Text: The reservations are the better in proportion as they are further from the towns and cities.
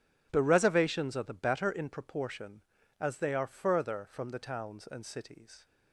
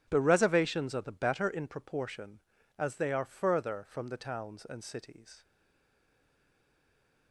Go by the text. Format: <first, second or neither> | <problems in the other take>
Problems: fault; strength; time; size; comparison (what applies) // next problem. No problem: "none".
first | stays silent after the last word; noticeable; from 5.4 s on; 1.9 s long